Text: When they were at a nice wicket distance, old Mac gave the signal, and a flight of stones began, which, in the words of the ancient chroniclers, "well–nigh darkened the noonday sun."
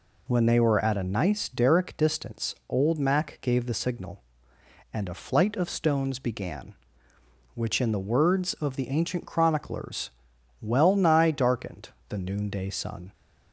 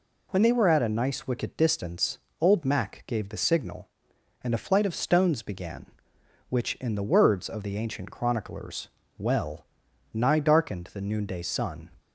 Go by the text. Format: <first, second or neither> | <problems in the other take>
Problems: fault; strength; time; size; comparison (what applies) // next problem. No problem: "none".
second | says "derrick" for "wicket"; at 1.4 s // pauses between "darkened" and "the"; slight; at 11.8 s; 0.20 s long